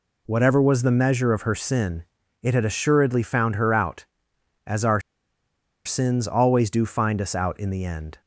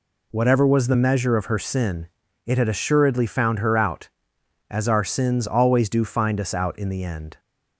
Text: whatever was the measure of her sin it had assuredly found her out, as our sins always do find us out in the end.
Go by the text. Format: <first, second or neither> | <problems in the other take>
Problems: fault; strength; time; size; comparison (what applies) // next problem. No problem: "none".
second | pauses between "sin" and "it"; at 2.0 s; 0.40 s long; also in the second // pauses between "our" and "sins"; noticeable; at 5.0 s; 0.85 s long